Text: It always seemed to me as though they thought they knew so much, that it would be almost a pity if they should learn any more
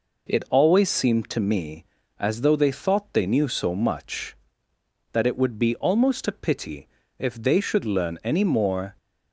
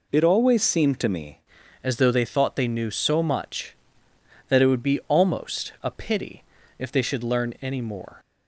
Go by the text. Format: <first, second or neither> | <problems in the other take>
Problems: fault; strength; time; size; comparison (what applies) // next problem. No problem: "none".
first | changes voice at "as"; from 1.8 s on; 6.3 s long // pauses between "pity" and "if"; slight; at 6.4 s; 0.36 s long; slight in the first